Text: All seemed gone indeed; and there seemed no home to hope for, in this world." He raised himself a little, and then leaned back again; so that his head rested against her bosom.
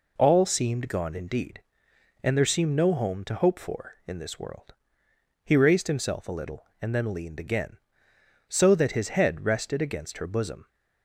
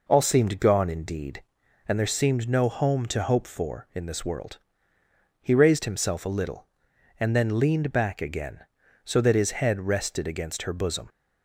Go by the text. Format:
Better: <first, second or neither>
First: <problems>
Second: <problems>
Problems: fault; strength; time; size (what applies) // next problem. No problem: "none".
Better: second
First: skips "back"; at 7.3 s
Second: none